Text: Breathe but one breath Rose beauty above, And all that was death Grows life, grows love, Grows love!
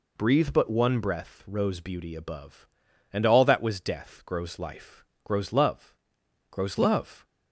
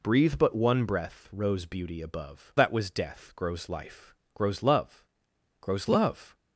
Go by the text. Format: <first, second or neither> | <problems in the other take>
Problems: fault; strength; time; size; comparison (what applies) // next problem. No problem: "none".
first | skips "And all"; at 2.5 s